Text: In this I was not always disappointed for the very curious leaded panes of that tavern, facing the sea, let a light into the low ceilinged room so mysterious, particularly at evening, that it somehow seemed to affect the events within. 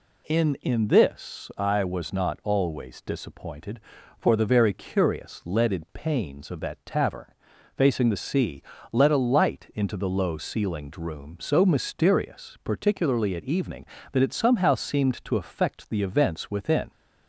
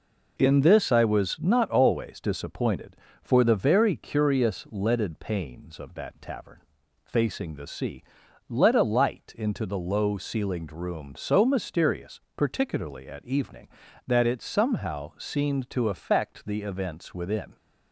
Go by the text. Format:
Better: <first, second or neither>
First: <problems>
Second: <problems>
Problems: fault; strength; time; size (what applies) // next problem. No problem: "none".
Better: second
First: says "In" twice; at 0.6 s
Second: none